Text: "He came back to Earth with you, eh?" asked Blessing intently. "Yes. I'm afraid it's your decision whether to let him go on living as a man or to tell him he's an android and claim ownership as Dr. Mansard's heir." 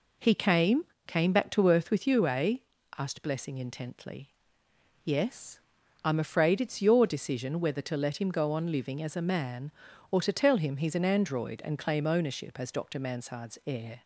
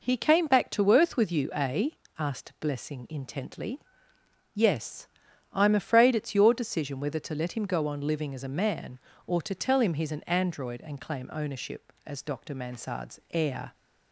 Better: second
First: says "came" twice; at 1.0 s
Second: none

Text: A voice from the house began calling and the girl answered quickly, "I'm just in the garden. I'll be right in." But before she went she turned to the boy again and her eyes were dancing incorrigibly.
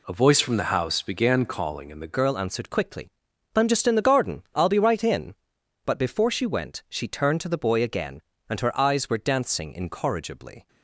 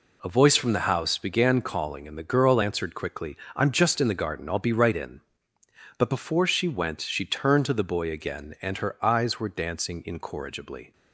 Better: second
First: changes voice at "girl"; from 2.1 s on; 8.5 s long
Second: none

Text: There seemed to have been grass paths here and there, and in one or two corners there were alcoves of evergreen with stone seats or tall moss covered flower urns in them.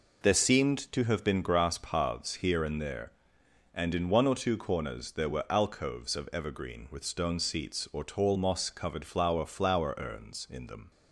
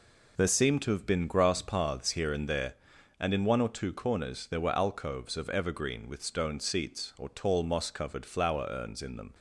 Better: second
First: says "flower" twice; at 9.4 s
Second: none

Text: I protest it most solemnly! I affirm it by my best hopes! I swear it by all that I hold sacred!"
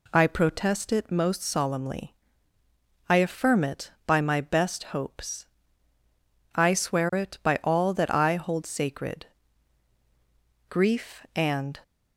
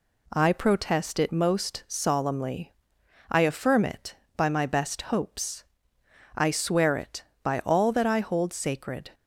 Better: second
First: goes on to say "Grief and"; noticeable; from 10.6 s on; 1.1 s long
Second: none

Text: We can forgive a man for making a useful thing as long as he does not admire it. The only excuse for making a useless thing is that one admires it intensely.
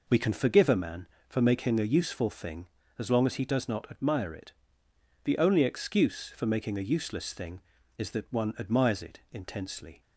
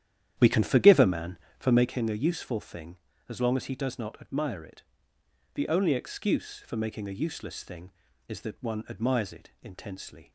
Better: first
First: none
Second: starts louder than the rest; strong; until 2.0 s; 10.5 dB

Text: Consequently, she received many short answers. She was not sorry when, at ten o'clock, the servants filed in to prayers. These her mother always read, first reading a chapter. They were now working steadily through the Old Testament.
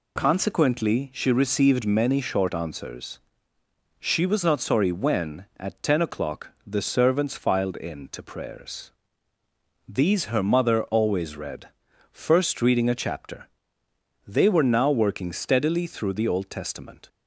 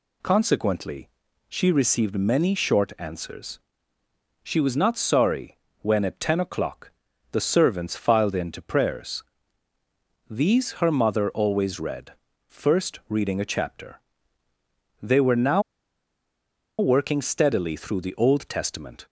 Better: first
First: none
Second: pauses between "sorry" and "when"; slight; at 5.5 s; 0.24 s long // pauses between "now" and "working"; at 15.6 s; 1.1 s long

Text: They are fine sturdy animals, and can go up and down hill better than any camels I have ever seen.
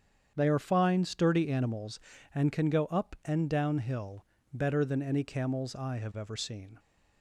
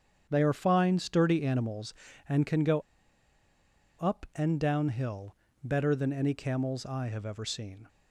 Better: first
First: starts louder than the rest; strong; until 1.3 s; 8 dB // pauses between "hill" and "better"; slight; at 4.2 s; 0.26 s long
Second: starts louder than the rest; strong; until 1.3 s; 8 dB // pauses between "go" and "up"; at 2.7 s; 1.1 s long // pauses between "hill" and "better"; slight; at 5.3 s; 0.26 s long

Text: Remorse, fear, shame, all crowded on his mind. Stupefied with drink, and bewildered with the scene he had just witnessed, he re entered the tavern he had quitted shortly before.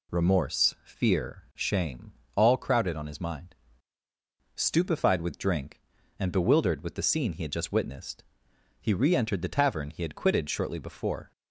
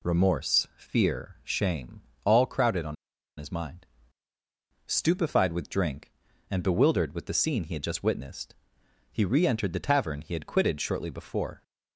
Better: first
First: none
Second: pauses between "on" and "his"; at 2.9 s; 0.43 s long

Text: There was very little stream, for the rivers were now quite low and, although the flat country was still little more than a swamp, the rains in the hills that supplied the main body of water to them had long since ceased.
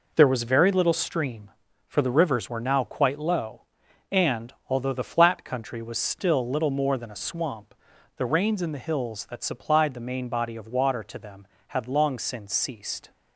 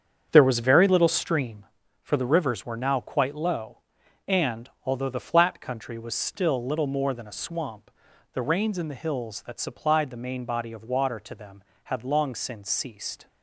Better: first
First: none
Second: starts louder than the rest; strong; until 1.7 s; 7.5 dB

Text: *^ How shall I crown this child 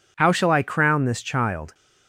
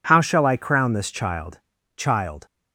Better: first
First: none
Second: says "child" twice; at 1.9 s

